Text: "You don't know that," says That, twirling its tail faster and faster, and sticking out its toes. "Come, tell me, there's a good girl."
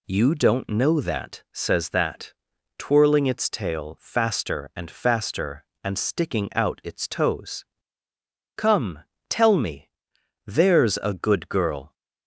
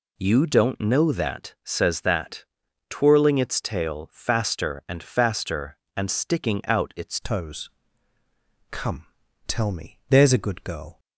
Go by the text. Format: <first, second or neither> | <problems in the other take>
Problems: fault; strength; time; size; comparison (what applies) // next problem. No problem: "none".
first | changes voice at "toes"; from 7.2 s on; 3.7 s long